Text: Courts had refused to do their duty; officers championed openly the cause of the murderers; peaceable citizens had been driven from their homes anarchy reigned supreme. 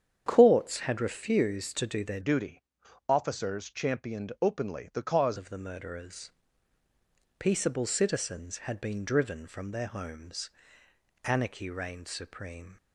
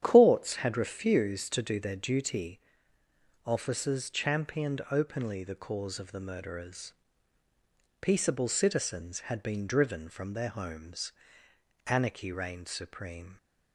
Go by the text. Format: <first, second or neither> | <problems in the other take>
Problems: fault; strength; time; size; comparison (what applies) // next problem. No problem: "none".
second | starts louder than the rest; strong; until 1.2 s; 8.5 dB; strong in the second // changes voice from "duty" to "cause"; from 2.2 to 5.3 s; 3.1 s long // pauses between "homes" and "anarchy"; noticeable; at 10.5 s; 0.74 s long; noticeable in the second